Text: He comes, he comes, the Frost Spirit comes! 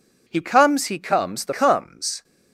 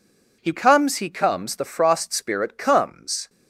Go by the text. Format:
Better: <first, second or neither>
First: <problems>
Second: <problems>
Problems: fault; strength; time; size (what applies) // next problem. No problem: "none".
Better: second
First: skips "Frost Spirit"; at 1.5 s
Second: none